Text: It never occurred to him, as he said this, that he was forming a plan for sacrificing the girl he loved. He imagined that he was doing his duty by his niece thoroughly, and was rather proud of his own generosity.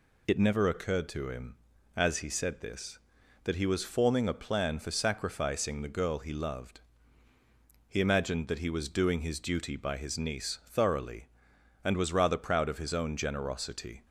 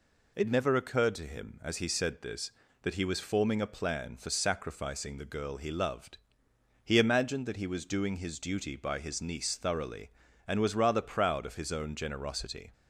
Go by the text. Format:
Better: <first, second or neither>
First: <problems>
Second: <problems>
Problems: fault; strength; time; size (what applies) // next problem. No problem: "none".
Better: neither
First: none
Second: none